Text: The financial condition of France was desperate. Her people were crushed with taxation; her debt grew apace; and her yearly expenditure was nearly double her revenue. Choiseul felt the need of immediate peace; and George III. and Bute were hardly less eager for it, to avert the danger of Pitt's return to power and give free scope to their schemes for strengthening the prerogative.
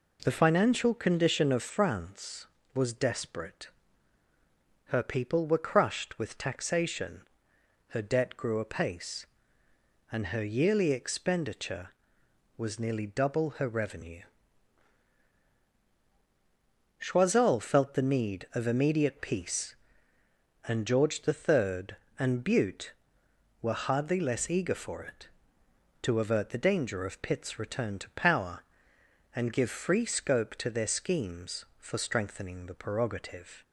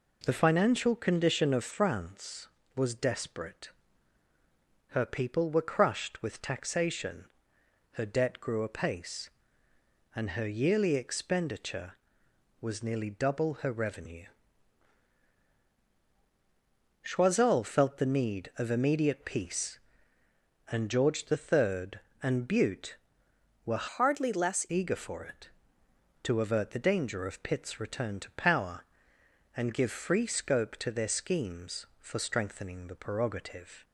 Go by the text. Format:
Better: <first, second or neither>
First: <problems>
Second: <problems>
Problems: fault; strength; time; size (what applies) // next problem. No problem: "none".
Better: first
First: none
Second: changes voice from "hardly" to "less"; from 23.8 to 24.6 s; 0.8 s long